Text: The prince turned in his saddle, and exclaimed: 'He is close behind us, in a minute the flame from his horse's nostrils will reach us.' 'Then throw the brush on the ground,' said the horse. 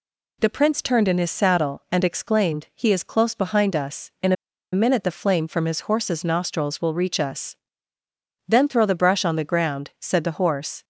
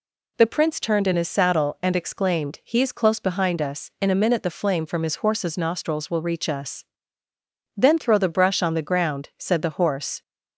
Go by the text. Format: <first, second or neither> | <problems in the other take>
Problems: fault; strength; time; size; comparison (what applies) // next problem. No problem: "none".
second | pauses between "a" and "minute"; at 4.3 s; 0.38 s long